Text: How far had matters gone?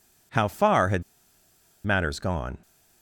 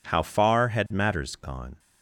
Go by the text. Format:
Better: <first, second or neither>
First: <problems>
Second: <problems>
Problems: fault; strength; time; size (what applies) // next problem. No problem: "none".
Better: second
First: pauses between "had" and "matters"; noticeable; at 1.0 s; 0.81 s long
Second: none